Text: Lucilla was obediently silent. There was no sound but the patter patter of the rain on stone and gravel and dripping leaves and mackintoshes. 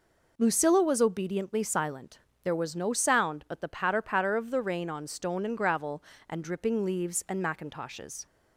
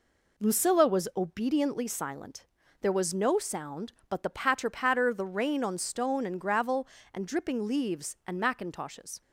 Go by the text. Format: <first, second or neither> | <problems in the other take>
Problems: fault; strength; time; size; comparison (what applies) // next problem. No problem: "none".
first | skips "of"; at 5.1 s